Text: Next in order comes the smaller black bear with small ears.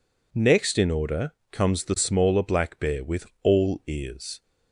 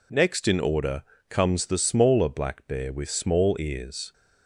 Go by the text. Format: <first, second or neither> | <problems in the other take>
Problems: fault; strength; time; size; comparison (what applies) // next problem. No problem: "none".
second | pauses between "order" and "comes"; slight; at 1.3 s; 0.18 s long; slight in the second // says "all" for "small"; at 3.4 s